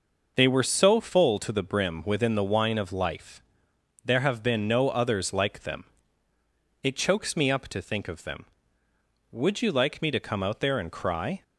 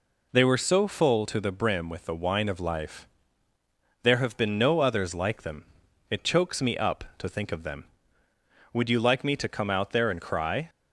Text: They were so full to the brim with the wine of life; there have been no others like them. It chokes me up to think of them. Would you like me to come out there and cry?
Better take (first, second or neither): second